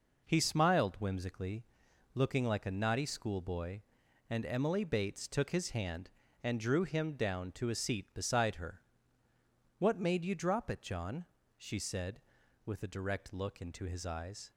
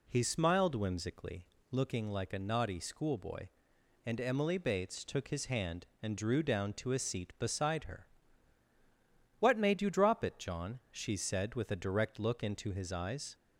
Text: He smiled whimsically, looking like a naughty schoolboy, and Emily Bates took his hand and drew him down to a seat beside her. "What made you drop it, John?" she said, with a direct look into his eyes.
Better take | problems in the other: first | skips "him"; at 6.4 s

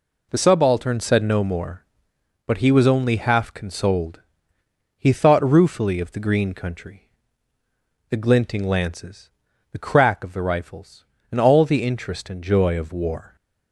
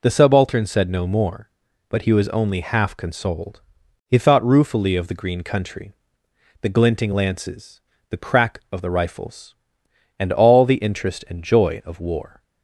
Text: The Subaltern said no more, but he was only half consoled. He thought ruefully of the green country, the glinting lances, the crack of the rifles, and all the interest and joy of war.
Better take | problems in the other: neither | none

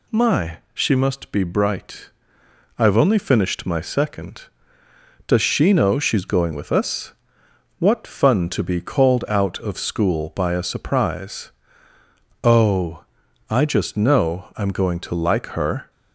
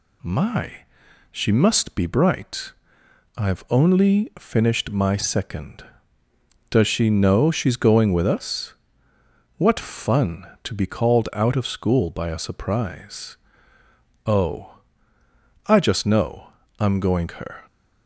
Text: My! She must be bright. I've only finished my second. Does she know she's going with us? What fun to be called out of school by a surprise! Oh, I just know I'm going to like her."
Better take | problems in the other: first | pauses between "know" and "I'm"; slight; at 16.4 s; 0.30 s long // skips "to like"; at 17.3 s

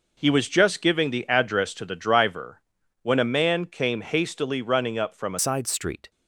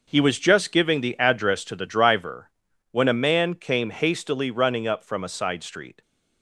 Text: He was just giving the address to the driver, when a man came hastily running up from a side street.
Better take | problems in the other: second | changes voice at "side"; from 5.3 s on; 0.8 s long

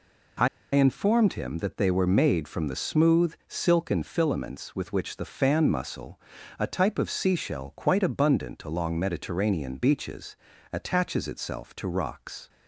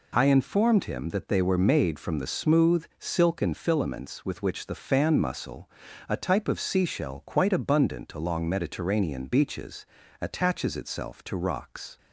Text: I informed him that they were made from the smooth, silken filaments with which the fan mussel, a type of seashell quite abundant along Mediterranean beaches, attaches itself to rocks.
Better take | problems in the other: second | pauses between "I" and "informed"; slight; at 0.4 s; 0.26 s long

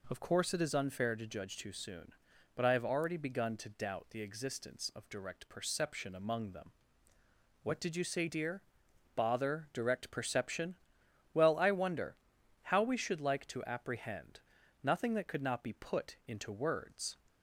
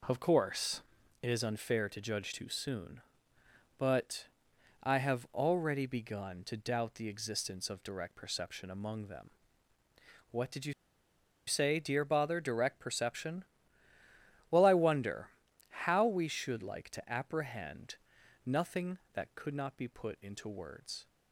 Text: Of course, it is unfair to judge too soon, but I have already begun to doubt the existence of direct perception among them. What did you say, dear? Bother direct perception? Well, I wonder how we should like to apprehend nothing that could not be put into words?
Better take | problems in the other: first | pauses between "but" and "I"; noticeable; at 4.2 s; 0.56 s long // pauses between "you" and "say"; noticeable; at 10.7 s; 0.73 s long // pauses between "wonder" and "how"; at 15.2 s; 0.40 s long; noticeable in the first // pauses between "apprehend" and "nothing"; noticeable; at 17.9 s; 0.50 s long; also in the first

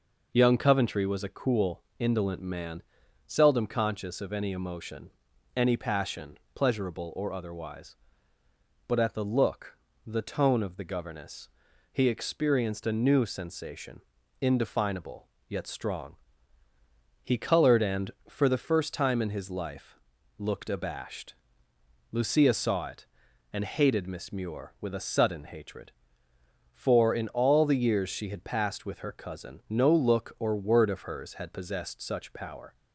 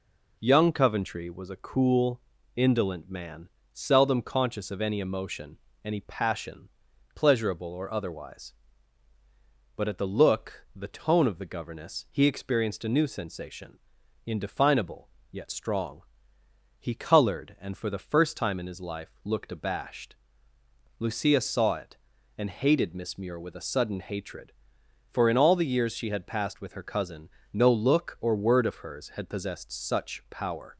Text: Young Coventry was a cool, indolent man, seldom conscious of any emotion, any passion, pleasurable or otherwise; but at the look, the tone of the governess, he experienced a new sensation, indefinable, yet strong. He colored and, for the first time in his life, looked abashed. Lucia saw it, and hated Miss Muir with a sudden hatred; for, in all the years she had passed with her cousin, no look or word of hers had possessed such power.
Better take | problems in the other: neither | none

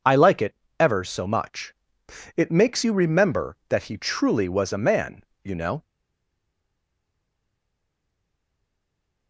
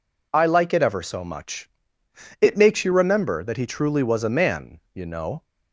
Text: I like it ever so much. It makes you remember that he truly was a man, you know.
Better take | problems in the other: second | pauses between "it" and "ever"; slight; at 0.5 s; 0.24 s long // stays silent after the last word; strong; from 5.8 s on; 3.4 s long

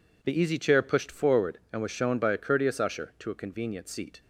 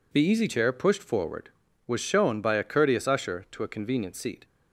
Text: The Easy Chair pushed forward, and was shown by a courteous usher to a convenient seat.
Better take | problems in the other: first | skips "and"; at 1.6 s

